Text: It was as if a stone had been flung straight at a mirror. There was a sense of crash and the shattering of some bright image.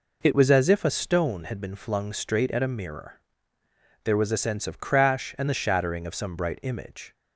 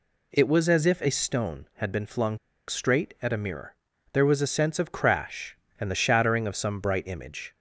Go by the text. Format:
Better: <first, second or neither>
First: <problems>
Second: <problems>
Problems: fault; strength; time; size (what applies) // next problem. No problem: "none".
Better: first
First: none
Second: pauses between "flung" and "straight"; slight; at 2.3 s; 0.30 s long